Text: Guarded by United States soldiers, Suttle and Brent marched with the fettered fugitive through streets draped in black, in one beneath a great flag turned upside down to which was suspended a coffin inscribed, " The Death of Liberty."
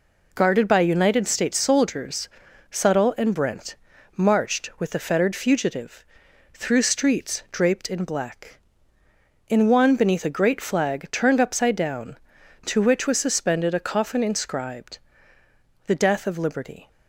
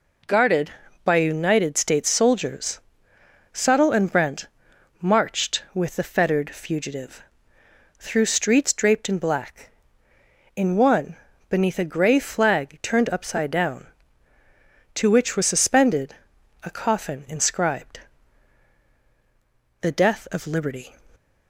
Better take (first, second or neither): first